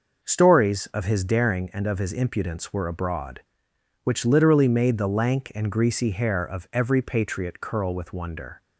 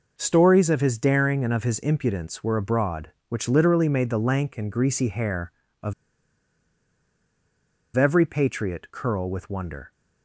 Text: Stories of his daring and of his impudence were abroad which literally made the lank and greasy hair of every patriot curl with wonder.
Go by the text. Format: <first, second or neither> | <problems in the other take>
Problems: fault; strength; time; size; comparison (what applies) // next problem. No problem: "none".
first | pauses between "of" and "every"; strong; at 5.9 s; 2.0 s long